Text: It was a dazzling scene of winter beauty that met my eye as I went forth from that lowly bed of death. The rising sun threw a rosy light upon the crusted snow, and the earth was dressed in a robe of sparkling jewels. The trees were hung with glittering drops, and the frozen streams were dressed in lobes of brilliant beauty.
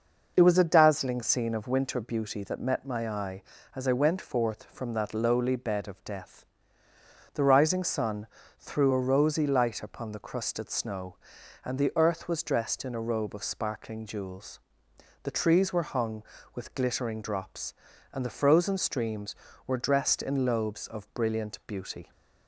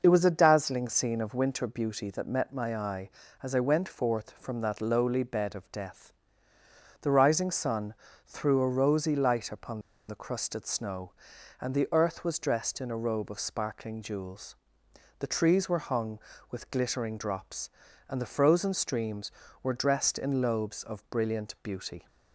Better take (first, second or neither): first